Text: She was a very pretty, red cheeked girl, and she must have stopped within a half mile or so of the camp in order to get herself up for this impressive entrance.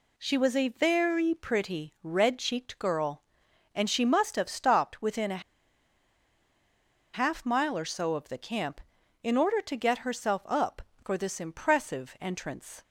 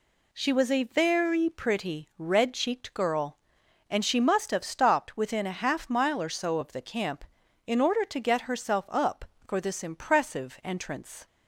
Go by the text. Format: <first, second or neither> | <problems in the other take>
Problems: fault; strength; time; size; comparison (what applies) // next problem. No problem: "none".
second | pauses between "a" and "half"; strong; at 5.4 s; 1.7 s long